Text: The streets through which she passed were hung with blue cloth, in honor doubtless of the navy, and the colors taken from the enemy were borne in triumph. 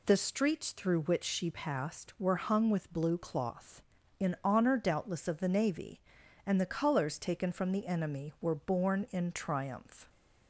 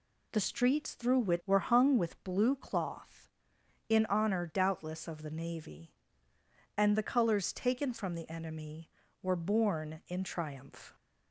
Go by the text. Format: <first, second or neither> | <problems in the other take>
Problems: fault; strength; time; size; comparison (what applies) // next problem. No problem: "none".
first | skips "she passed"; at 1.4 s